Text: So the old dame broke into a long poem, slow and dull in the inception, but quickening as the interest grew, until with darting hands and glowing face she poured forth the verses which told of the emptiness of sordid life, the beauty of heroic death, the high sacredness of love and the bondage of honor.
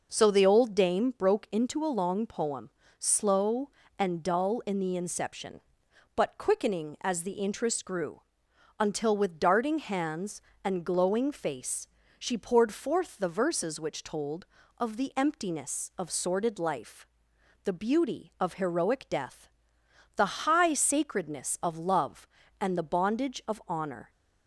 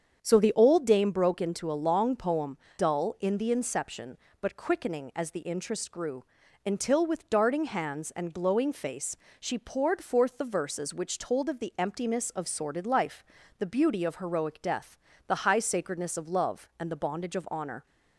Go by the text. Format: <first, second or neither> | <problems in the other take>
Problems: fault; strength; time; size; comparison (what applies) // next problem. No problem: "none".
first | starts louder than the rest; strong; until 1.2 s; 7.5 dB // skips "slow and"; at 2.6 s // pauses between "face" and "she"; slight; at 9.1 s; 0.24 s long; slight in the first